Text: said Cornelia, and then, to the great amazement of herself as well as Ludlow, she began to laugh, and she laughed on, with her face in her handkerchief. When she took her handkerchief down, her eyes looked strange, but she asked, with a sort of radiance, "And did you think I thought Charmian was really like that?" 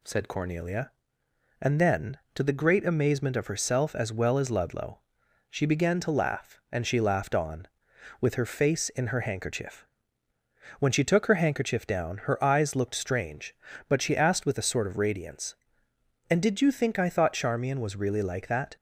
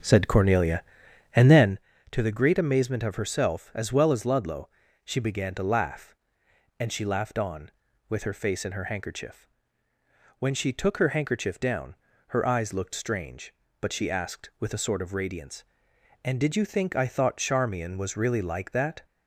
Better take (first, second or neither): first